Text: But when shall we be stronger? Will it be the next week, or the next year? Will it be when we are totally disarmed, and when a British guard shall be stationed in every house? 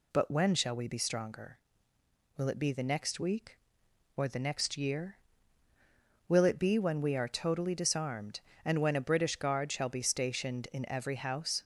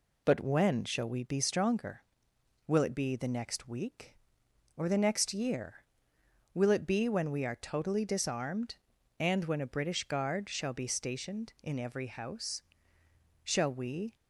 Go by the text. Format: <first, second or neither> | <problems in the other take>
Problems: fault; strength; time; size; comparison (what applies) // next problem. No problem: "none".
first | goes on to say "Shall we"; noticeable; from 13.4 s on; 0.72 s long